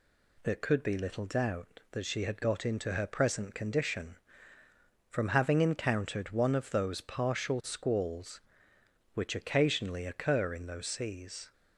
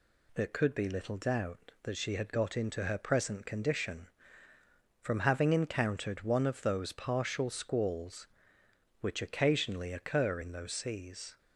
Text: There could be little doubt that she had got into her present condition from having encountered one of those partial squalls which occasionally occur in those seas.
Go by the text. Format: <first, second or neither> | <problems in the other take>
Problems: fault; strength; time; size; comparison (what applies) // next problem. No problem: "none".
neither | none